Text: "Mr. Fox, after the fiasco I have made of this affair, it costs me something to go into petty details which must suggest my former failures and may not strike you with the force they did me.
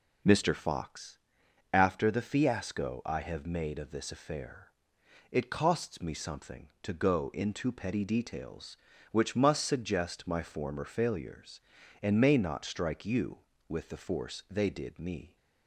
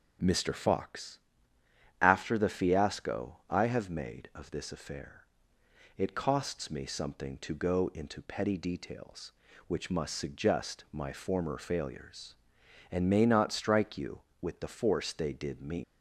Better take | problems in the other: first | starts louder than the rest; noticeable; until 2.0 s; 6 dB // leaves "me" unfinished; at 15.8 s; 180 ms

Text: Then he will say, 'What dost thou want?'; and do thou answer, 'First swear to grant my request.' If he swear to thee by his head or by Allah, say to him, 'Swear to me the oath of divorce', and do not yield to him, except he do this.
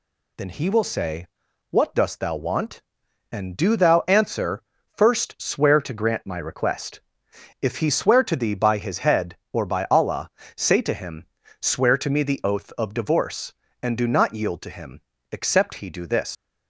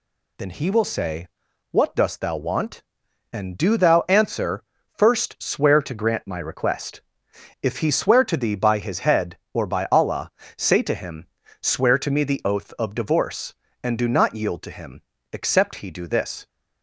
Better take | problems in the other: second | leaves "this" unfinished; at 16.3 s; 110 ms

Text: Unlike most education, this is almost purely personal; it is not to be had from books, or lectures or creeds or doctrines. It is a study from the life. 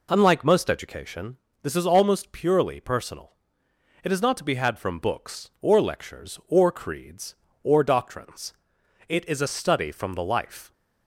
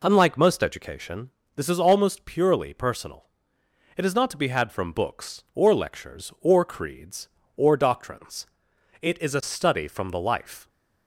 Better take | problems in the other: neither | none

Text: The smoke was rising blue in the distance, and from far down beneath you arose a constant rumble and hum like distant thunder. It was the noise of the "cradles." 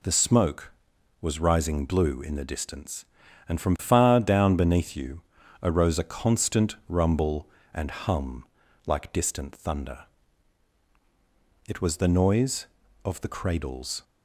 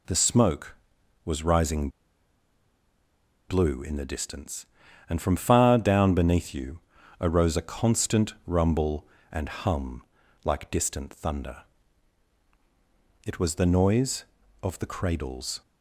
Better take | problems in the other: first | pauses between "rising" and "blue"; strong; at 1.8 s; 1.6 s long // pauses between "you" and "arose"; at 6.7 s; 0.42 s long; also in the first // pauses between "hum" and "like"; at 10.0 s; 0.40 s long; also in the first

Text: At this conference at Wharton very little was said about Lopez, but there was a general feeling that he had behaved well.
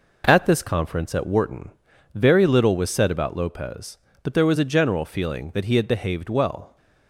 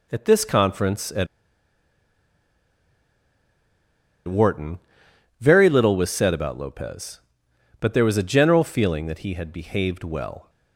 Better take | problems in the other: first | pauses between "at" and "Wharton"; strong; at 1.2 s; 3.0 s long // pauses between "Wharton" and "very"; noticeable; at 4.7 s; 0.60 s long; noticeable in the first

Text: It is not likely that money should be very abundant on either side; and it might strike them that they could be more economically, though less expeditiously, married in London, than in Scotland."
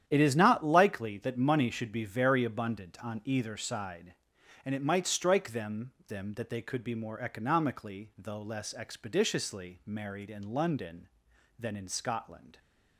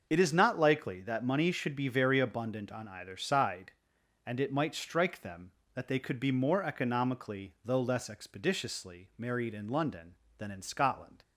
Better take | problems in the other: second | starts louder than the rest; strong; until 1.0 s; 10 dB; also in the second // says "them" twice; at 6.0 s

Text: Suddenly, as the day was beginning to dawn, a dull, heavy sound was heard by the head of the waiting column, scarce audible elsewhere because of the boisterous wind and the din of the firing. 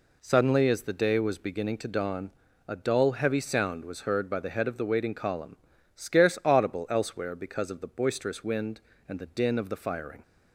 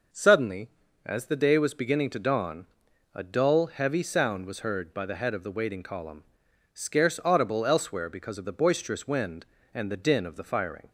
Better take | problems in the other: neither | none

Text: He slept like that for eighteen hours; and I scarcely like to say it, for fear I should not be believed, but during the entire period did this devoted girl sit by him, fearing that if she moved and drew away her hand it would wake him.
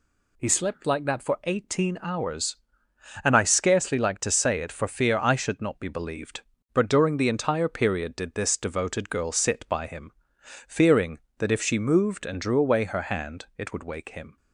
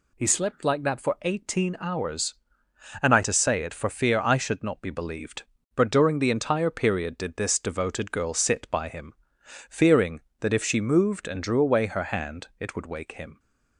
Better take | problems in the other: first | skips "scarcely like"; at 3.2 s

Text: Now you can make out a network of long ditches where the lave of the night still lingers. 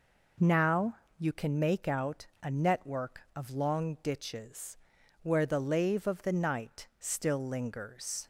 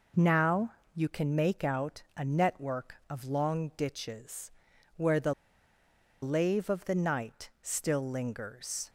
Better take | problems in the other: first | pauses between "Now" and "you"; slight; at 0.7 s; 0.24 s long; slight in the first // pauses between "ditches" and "where"; at 4.5 s; 0.44 s long; also in the first // pauses between "the" and "lave"; noticeable; at 5.3 s; 0.89 s long

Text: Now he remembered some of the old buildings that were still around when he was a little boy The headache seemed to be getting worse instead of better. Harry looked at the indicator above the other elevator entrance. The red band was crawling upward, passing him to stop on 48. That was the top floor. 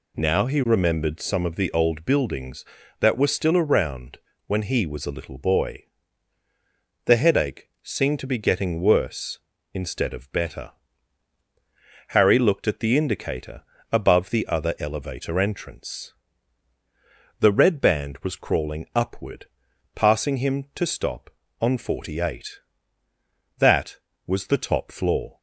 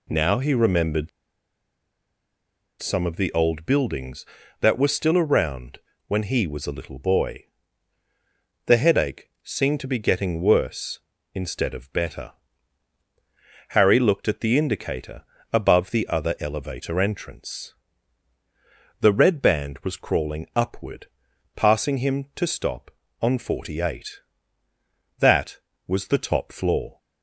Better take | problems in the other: first | pauses between "remembered" and "some"; strong; at 1.0 s; 1.7 s long // pauses between "around" and "when"; slight; at 5.7 s; 0.30 s long; slight in the first // pauses between "boy" and "The"; at 7.4 s; 1.2 s long; also in the first // pauses between "indicator" and "above"; slight; at 15.2 s; 0.32 s long; slight in the first

